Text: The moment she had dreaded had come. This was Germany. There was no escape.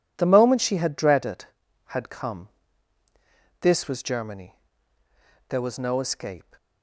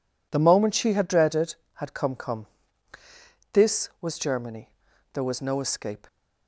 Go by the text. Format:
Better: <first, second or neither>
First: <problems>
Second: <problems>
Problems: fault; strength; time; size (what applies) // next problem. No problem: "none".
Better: first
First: none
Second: says "come" twice; at 2.1 s